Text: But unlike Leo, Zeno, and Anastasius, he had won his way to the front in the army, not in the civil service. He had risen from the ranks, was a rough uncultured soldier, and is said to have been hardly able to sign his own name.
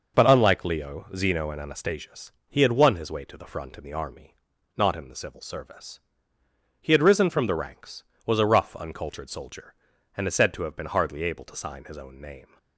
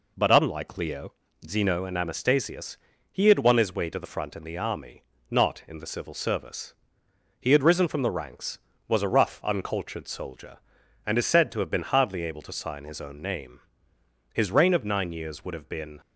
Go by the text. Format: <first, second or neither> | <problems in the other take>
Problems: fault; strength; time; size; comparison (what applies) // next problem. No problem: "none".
first | goes on to say "His reign of nine years would have been"; strong; from 14.3 s on; 1.6 s long